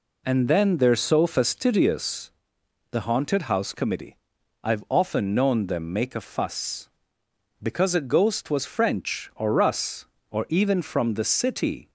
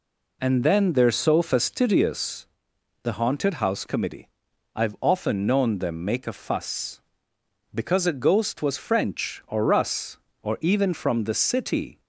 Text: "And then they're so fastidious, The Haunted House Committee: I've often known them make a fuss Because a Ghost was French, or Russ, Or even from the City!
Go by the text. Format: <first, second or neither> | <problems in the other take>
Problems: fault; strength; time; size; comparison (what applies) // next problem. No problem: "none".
neither | none